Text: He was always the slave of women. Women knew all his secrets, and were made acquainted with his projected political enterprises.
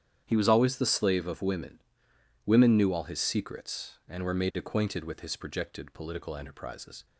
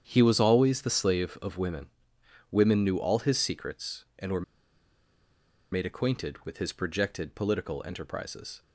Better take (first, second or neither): first